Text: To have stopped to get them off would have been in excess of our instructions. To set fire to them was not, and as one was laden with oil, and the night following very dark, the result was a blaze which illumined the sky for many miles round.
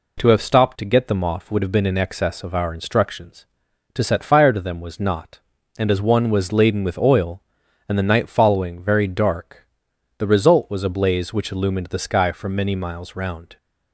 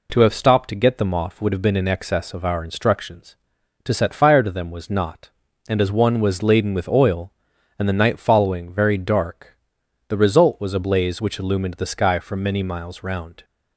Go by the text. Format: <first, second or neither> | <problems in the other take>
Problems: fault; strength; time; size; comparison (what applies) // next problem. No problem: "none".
neither | none